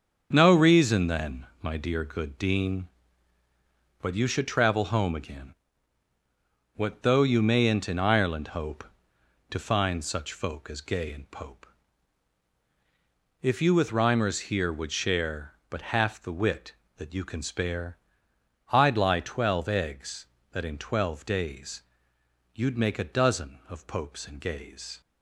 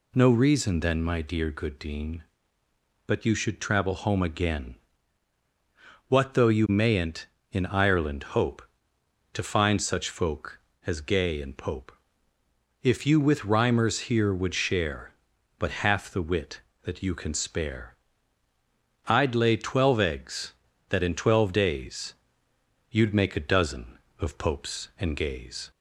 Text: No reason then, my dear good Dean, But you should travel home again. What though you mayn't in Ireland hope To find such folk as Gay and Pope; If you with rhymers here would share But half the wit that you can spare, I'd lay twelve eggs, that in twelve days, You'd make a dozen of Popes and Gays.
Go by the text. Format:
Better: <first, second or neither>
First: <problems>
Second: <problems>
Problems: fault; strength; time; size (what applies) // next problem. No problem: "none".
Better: second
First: starts louder than the rest; until 1.3 s; 7 dB // says "lie" for "lay"; at 18.9 s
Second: none